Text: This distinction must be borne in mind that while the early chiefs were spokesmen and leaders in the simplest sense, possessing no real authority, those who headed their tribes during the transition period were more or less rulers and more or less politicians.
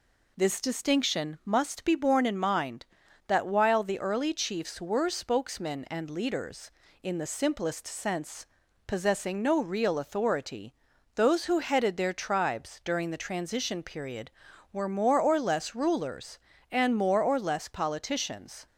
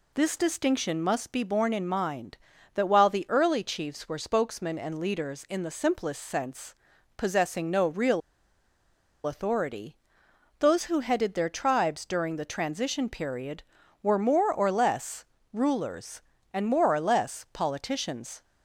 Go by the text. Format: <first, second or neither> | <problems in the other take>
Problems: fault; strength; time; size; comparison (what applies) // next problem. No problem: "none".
first | pauses between "real" and "authority"; at 8.2 s; 1.0 s long // pauses between "less" and "rulers"; slight; at 15.2 s; 0.28 s long